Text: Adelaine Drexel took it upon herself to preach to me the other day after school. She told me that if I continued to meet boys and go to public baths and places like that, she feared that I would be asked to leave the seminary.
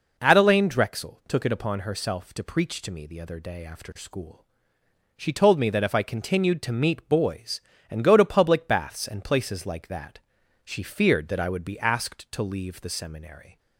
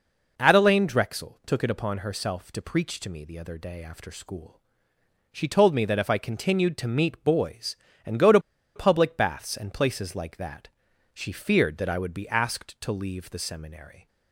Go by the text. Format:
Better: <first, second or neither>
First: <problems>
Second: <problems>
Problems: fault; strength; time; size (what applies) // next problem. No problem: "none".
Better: first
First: none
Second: pauses between "to" and "public"; at 8.3 s; 0.36 s long